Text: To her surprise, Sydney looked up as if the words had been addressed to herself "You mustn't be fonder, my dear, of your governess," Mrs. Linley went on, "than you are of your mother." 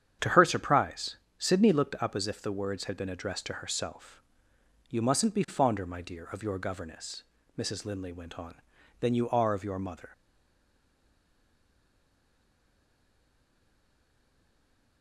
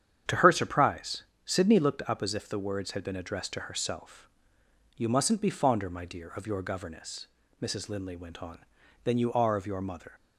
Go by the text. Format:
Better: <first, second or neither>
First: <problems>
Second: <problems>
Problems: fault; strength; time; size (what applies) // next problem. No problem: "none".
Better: second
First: starts louder than the rest; strong; until 1.4 s; 9 dB // pauses between "herself" and "You"; noticeable; at 4.2 s; 0.68 s long // stays silent after the last word; strong; from 10.1 s on; 4.9 s long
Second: starts louder than the rest; strong; until 1.5 s; 9 dB // pauses between "herself" and "You"; noticeable; at 4.2 s; 0.68 s long